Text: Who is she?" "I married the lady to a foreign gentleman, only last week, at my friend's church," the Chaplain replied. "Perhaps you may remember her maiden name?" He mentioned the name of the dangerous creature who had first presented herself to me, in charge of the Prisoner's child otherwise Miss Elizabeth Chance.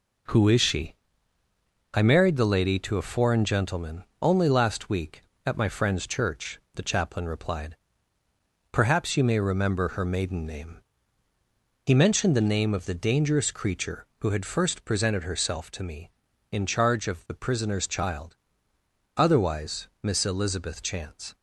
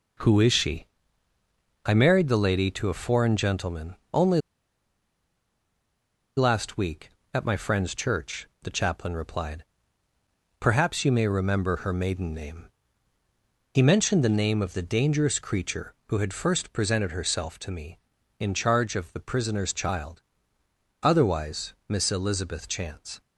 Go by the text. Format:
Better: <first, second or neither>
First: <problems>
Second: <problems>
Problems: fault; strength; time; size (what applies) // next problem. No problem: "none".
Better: first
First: pauses between "child" and "otherwise"; noticeable; at 18.3 s; 0.80 s long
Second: pauses between "only" and "last"; strong; at 4.4 s; 1.9 s long // pauses between "child" and "otherwise"; noticeable; at 20.2 s; 0.80 s long